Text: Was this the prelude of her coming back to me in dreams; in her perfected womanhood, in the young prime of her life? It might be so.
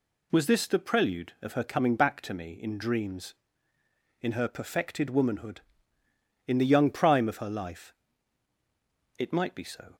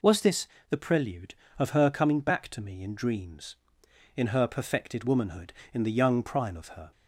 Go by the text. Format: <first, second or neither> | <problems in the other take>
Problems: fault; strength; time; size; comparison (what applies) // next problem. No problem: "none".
first | pauses between "this" and "the"; slight; at 0.4 s; 0.22 s long // stops before "life It might be so"; at 6.9 s